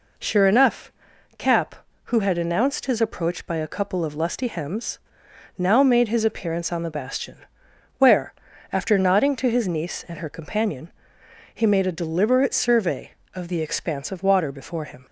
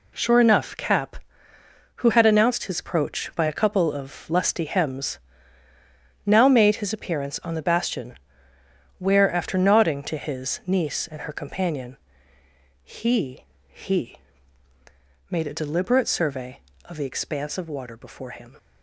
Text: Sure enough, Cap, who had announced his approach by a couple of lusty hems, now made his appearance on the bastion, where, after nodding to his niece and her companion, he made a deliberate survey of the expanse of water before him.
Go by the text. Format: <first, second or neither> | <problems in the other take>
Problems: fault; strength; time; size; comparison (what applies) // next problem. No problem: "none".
first | says "he" twice; at 13.6 s